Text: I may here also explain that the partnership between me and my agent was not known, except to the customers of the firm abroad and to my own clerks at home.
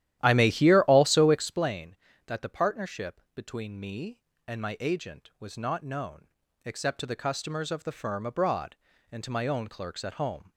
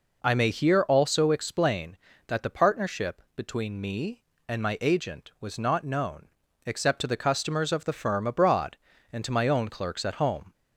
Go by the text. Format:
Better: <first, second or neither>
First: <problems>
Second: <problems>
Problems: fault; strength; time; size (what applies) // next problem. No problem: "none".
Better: second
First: starts louder than the rest; strong; until 1.7 s; 12.5 dB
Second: none